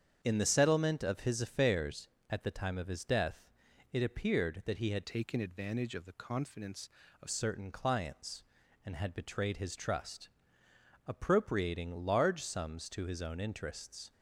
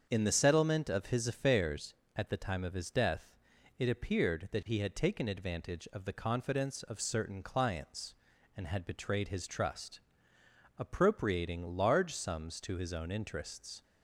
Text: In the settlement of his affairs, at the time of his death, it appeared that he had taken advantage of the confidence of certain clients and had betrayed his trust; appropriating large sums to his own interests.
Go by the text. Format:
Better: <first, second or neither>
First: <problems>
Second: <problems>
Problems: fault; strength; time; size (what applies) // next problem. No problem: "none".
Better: second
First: starts louder than the rest; strong; until 1.2 s; 8 dB // changes voice from "taken" to "of"; from 5.0 to 7.2 s; 2.2 s long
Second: starts louder than the rest; until 1.1 s; 7 dB